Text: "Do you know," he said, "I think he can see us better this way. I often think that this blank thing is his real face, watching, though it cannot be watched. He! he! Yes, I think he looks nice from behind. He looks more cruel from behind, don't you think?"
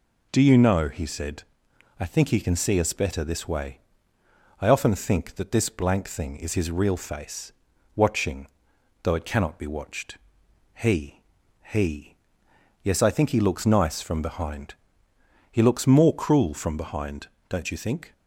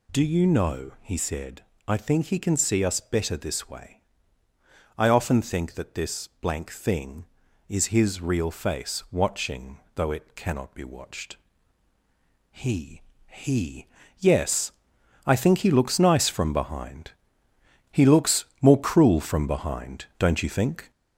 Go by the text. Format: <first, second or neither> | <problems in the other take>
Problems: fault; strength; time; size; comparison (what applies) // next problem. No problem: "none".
first | gets louder; throughout; 4 dB